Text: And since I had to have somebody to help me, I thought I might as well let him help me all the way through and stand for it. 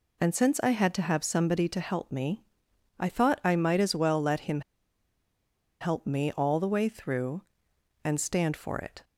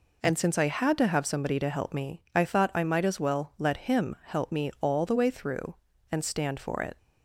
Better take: second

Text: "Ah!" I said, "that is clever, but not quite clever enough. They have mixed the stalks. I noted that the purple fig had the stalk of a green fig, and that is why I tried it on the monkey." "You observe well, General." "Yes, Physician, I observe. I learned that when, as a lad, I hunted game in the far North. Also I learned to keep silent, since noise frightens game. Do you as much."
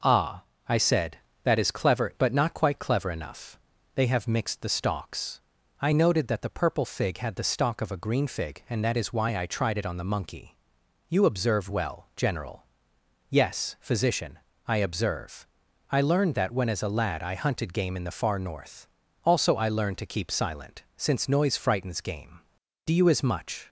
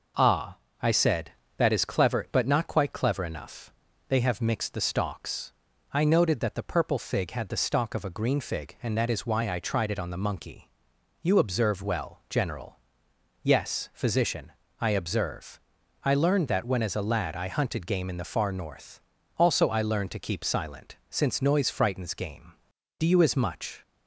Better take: neither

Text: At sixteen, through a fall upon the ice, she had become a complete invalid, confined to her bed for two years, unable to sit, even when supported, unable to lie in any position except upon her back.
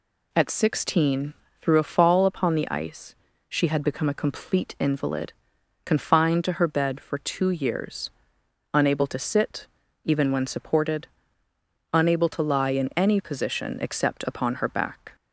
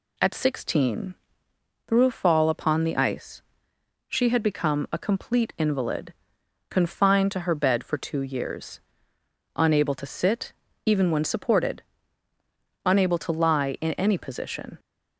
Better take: first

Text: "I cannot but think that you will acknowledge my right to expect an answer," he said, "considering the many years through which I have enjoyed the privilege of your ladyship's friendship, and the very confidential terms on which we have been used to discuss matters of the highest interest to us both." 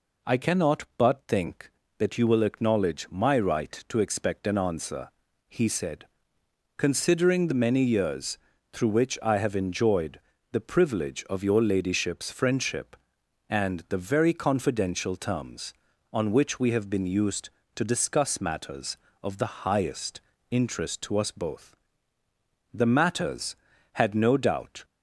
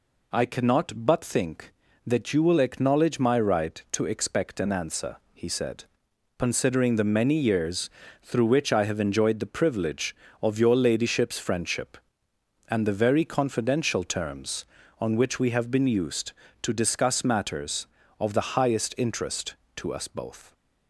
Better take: second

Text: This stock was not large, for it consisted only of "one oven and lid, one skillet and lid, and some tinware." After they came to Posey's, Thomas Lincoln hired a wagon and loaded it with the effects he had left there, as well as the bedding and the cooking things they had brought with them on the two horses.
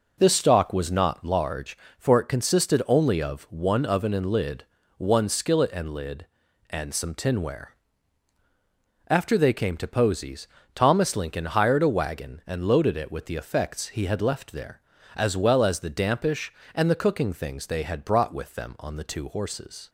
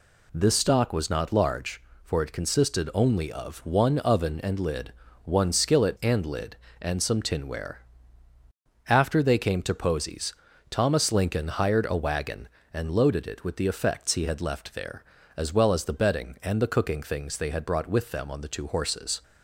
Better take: second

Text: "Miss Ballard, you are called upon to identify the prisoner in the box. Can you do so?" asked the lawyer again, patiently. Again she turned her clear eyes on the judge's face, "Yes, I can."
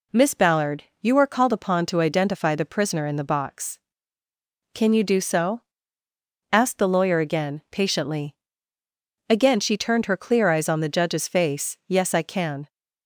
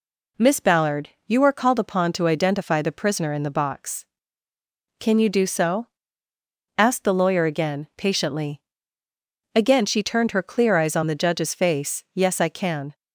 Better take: neither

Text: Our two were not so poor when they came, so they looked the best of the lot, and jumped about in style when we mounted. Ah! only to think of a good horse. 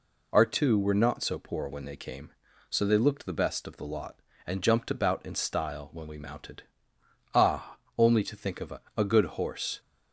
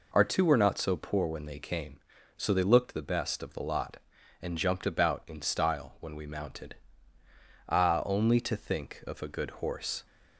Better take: second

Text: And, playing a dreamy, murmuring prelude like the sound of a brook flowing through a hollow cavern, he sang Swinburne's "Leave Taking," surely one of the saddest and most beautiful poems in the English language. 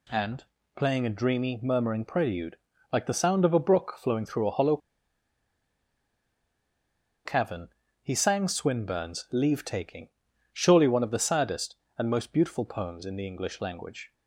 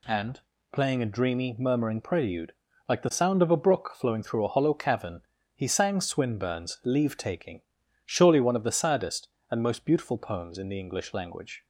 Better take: second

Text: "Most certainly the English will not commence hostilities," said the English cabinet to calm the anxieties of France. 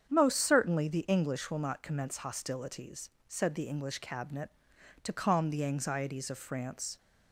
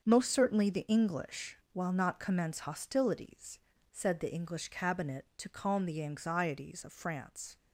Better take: first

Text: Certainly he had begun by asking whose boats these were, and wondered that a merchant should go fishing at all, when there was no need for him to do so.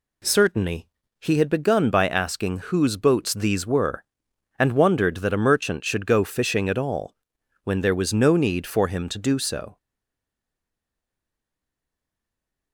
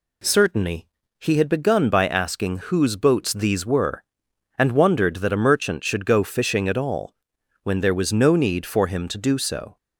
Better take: second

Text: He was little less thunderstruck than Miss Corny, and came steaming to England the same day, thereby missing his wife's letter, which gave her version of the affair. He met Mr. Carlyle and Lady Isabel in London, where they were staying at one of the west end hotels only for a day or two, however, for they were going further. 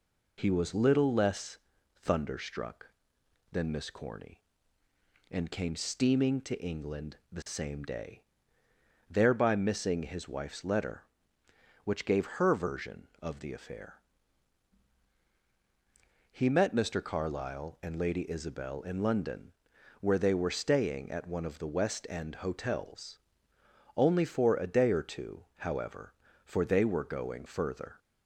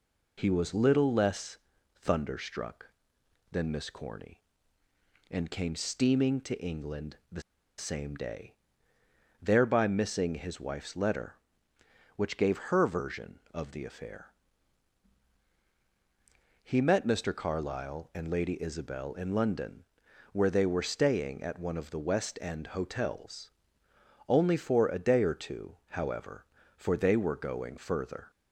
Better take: first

